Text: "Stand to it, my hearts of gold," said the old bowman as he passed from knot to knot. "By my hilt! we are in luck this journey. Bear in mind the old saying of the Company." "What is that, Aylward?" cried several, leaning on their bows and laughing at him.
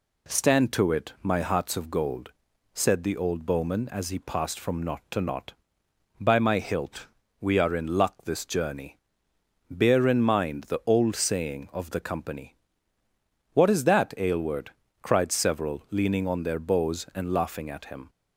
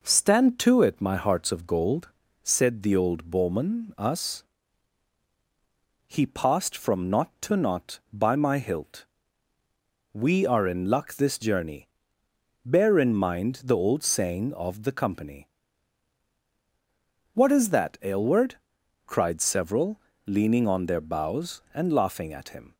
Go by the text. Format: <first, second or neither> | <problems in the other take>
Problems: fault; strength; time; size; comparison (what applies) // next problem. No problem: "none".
first | says "us" for "as"; at 3.9 s